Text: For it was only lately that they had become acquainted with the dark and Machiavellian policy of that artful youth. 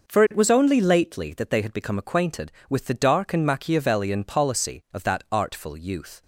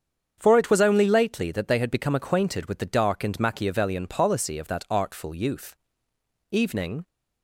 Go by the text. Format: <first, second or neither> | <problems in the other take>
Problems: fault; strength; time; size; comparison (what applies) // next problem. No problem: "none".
first | starts louder than the rest; strong; until 1.3 s; 7.5 dB // goes on to say "Evening"; from 6.5 s on; 0.56 s long